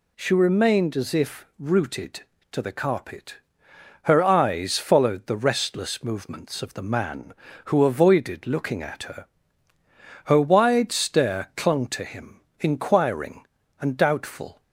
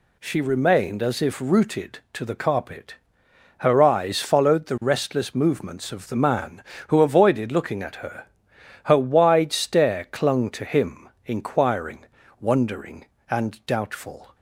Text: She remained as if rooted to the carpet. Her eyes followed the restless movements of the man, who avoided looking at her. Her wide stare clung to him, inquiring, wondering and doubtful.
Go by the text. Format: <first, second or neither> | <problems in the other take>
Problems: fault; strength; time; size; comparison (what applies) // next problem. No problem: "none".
second | skips "wondering"; at 13.6 s